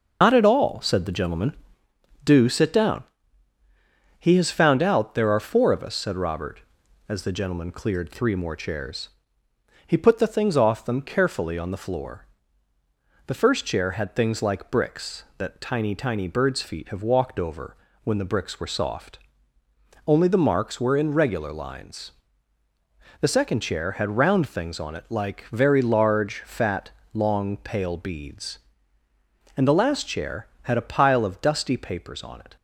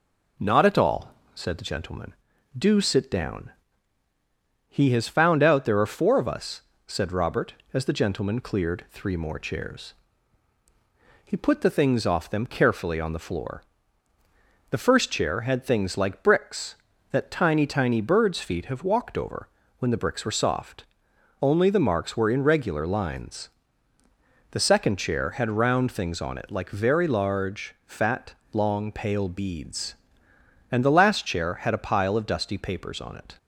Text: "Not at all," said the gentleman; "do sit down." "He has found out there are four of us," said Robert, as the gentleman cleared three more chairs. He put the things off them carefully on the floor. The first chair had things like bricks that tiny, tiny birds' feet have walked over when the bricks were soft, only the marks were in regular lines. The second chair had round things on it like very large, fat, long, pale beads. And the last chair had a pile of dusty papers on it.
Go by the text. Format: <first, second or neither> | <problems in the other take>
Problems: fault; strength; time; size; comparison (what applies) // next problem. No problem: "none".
second | loses the start of "Not"; at 0.2 s; 120 ms // pauses between "over" and "when"; slight; at 17.7 s; 0.26 s long; slight in the second